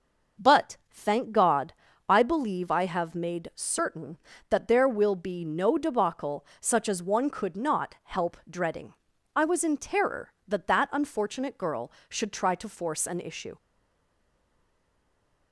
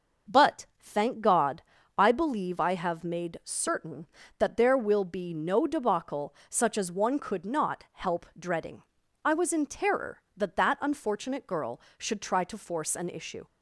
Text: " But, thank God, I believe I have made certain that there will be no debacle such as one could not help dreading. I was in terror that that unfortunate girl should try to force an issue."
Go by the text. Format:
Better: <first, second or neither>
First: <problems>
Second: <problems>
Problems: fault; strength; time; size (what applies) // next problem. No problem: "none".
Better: second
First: starts louder than the rest; noticeable; until 1.5 s; 6 dB // pauses between "debacle" and "such"; slight; at 6.4 s; 0.16 s long // stays silent after the last word; noticeable; from 13.5 s on; 2.0 s long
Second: starts louder than the rest; noticeable; until 1.4 s; 6 dB // pauses between "debacle" and "such"; slight; at 6.3 s; 0.16 s long